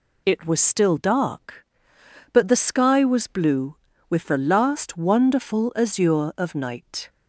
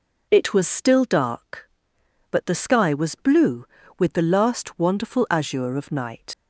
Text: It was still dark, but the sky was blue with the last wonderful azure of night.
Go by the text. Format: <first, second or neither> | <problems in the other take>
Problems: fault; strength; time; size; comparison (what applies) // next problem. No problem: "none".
first | leaves "night" unfinished; at 6.3 s; 105 ms